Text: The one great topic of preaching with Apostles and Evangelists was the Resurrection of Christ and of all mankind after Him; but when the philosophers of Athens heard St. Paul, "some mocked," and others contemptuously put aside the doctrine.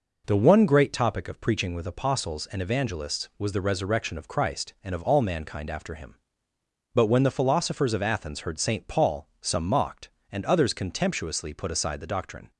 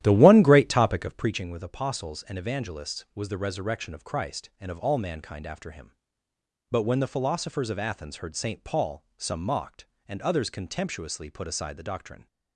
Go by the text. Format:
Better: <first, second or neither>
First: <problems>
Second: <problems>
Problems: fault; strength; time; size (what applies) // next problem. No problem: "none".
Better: first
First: none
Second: starts louder than the rest; strong; until 1.4 s; 12.5 dB